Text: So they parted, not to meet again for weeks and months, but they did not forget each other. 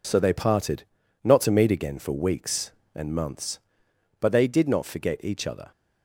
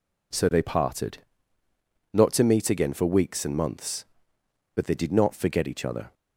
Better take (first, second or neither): neither